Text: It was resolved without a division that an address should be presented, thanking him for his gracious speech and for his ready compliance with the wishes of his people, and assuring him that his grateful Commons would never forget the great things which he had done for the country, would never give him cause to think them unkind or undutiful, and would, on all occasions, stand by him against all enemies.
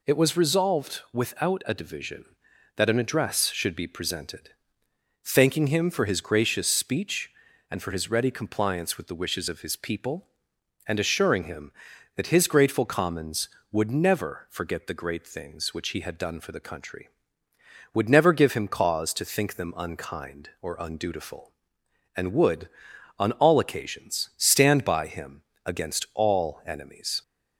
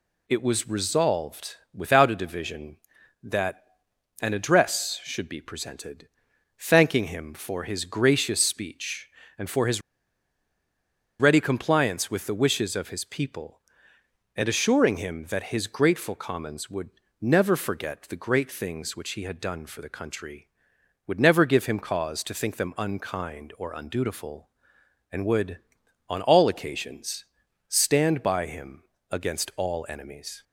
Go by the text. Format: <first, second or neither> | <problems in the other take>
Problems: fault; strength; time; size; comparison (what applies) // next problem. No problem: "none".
first | pauses between "resolved" and "without"; slight; at 1.5 s; 0.16 s long // pauses between "that" and "an"; noticeable; at 3.6 s; 0.56 s long // pauses between "his" and "ready"; strong; at 9.8 s; 1.3 s long // pauses between "would" and "never"; slight; at 16.8 s; 0.32 s long // pauses between "him" and "against"; slight; at 28.8 s; 0.28 s long; slight in the first